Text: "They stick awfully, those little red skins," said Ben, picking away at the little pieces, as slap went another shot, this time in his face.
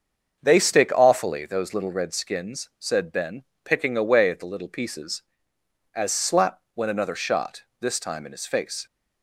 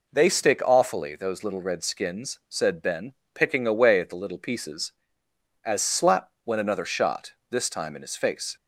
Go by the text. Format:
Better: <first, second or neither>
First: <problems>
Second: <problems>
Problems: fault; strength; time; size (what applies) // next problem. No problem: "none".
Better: second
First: starts louder than the rest; until 2.2 s; 6.5 dB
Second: none